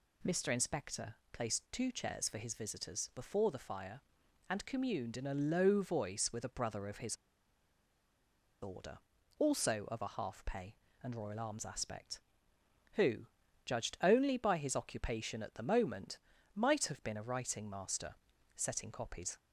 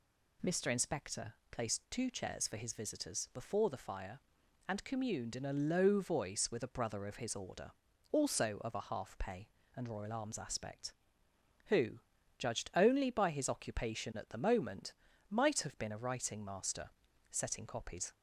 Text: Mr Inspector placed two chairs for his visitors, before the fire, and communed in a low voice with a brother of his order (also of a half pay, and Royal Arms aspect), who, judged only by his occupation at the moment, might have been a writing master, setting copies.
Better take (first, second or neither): second